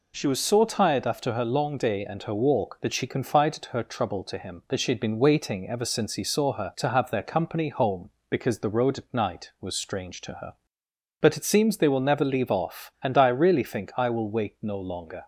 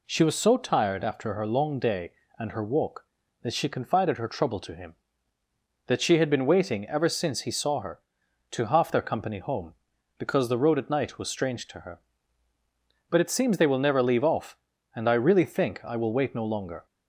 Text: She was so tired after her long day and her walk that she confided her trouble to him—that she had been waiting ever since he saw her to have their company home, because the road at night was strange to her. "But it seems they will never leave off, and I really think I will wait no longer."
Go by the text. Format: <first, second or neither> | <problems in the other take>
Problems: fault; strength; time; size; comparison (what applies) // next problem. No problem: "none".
first | says "half" for "have"; at 8.6 s